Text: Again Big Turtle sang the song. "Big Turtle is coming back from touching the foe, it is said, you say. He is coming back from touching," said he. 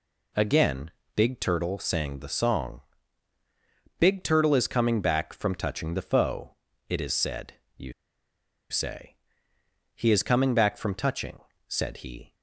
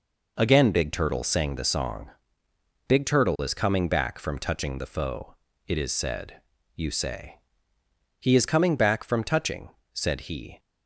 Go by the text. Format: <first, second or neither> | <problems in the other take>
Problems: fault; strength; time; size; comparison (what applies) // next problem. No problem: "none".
second | pauses between "Again" and "Big"; slight; at 0.9 s; 0.26 s long // pauses between "you" and "say"; noticeable; at 7.9 s; 0.77 s long